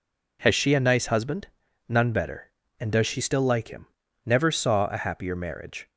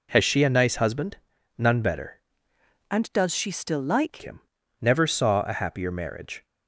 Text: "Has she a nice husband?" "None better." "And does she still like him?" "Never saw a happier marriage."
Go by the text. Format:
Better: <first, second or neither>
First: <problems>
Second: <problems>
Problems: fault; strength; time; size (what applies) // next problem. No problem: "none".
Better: first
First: none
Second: changes voice from "And" to "like"; from 2.8 to 4.2 s; 1.4 s long